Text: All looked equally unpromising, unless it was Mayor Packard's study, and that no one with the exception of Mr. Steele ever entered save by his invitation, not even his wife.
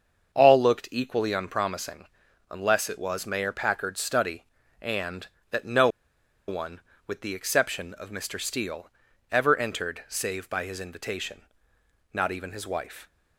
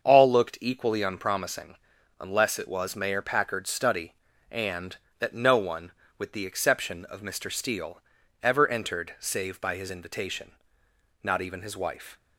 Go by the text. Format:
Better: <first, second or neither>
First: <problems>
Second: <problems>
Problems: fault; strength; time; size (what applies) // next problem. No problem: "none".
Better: second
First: starts louder than the rest; until 1.3 s; 7 dB // pauses between "no" and "one"; noticeable; at 5.8 s; 0.60 s long // pauses between "Steele" and "ever"; at 8.8 s; 0.42 s long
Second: starts louder than the rest; until 1.0 s; 6.5 dB // pauses between "Steele" and "ever"; at 8.0 s; 0.42 s long